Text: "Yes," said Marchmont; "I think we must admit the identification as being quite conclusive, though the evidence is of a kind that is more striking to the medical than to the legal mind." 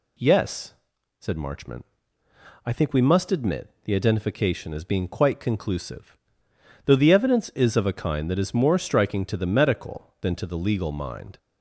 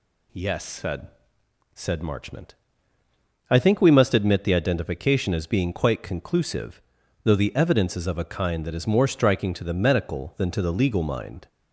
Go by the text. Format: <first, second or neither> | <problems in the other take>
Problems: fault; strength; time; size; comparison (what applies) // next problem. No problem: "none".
first | says "said" twice; at 1.7 s